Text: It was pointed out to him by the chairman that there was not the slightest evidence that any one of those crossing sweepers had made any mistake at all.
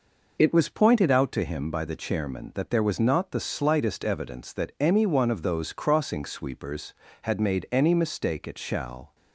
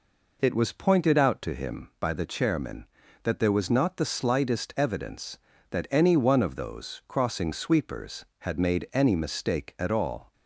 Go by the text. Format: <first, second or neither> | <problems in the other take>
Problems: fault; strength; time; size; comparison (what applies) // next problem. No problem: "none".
second | says "shall" for "all"; at 8.5 s